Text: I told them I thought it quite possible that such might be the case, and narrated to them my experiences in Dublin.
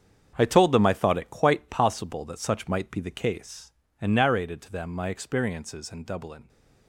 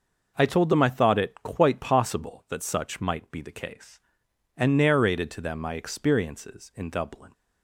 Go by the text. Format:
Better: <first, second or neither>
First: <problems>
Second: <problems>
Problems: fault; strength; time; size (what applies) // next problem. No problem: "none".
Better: second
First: gets quieter; strong; throughout; 10.5 dB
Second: none